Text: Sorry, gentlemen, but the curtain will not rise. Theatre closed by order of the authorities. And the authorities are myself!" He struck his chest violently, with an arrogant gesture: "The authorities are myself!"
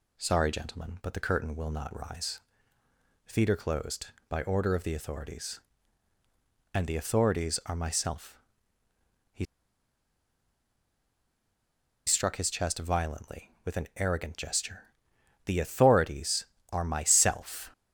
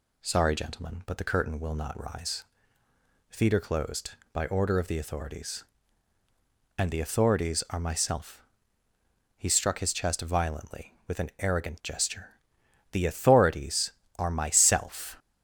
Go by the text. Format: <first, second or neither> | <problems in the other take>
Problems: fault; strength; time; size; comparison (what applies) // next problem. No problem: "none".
second | pauses between "He" and "struck"; strong; at 9.4 s; 2.6 s long